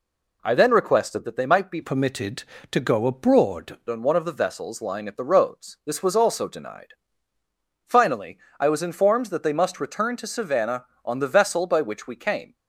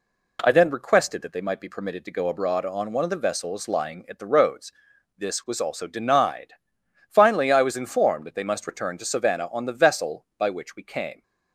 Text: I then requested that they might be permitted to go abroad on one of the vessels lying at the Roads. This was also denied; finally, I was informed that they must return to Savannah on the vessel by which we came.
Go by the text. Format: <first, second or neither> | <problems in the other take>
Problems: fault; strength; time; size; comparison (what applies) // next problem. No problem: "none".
second | changes voice from "permitted" to "abroad"; from 1.8 to 3.7 s; 1.9 s long